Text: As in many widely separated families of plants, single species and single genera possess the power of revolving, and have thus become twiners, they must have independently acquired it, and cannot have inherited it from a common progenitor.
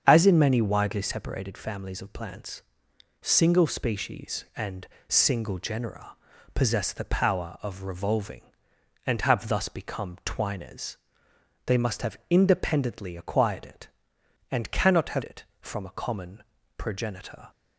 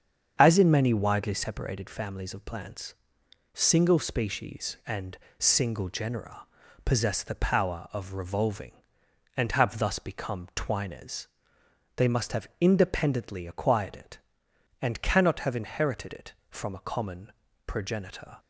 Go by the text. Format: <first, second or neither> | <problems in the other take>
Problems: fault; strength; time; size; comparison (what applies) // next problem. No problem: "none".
second | starts louder than the rest; strong; until 1.0 s; 7.5 dB; strong in the second // pauses between "and" and "single"; slight; at 4.8 s; 0.22 s long; slight in the second // pauses between "genera" and "possess"; at 6.1 s; 0.38 s long; also in the second // skips "inherited"; at 15.2 s // pauses between "common" and "progenitor"; slight; at 16.4 s; 0.34 s long; slight in the second